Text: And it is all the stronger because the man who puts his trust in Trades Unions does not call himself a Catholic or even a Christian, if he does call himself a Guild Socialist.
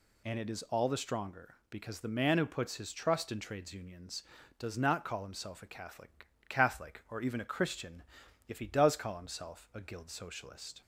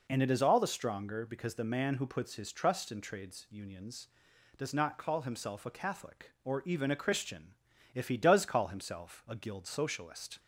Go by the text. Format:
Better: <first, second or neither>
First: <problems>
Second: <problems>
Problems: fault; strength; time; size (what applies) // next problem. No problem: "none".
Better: second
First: says "Catholic" twice; at 6.4 s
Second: none